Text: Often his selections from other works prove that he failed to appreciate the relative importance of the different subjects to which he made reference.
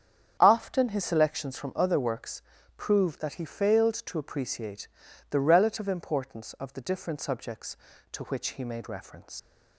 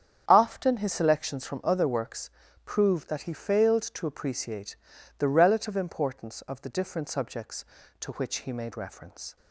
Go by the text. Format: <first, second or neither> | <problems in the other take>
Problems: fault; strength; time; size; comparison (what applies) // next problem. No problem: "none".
second | starts louder than the rest; strong; until 1.4 s; 8.5 dB; strong in the second // pauses between "works" and "prove"; slight; at 2.4 s; 0.34 s long; slight in the second // pauses between "appreciate" and "the"; at 4.8 s; 0.42 s long; also in the second // leaves "reference" unfinished; at 9.3 s; 75 ms